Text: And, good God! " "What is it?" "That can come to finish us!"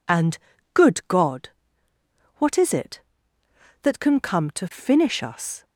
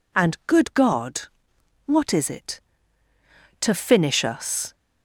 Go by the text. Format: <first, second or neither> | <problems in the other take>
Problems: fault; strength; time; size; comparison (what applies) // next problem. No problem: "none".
first | skips "That can come"; at 3.1 s